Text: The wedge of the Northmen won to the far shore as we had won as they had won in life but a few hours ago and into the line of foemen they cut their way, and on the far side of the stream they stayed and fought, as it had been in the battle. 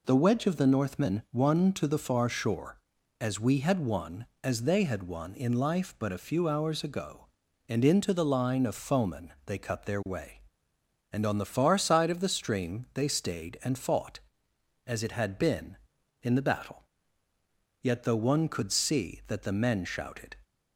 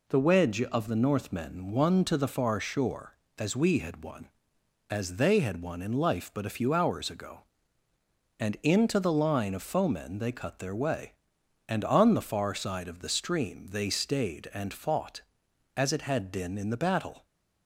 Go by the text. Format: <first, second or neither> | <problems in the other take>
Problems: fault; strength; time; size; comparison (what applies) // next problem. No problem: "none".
second | goes on to say "Yet though one could see that the men shouted"; strong; from 17.8 s on; 2.5 s long